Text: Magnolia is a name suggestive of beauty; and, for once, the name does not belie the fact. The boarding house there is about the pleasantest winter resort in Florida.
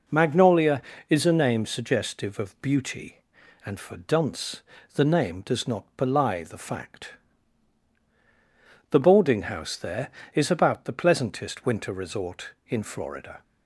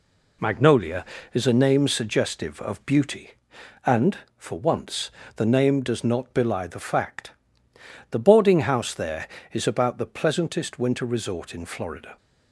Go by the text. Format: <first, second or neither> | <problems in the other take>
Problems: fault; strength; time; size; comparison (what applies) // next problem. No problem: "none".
second | says "dunce" for "once"; at 3.9 s